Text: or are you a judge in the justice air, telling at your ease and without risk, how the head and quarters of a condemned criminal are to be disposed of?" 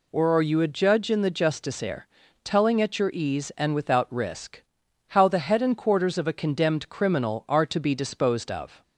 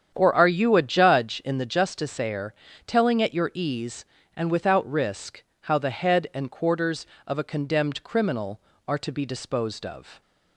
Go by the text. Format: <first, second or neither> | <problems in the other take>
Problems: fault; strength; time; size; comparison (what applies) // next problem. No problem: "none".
first | starts louder than the rest; strong; until 1.7 s; 8.5 dB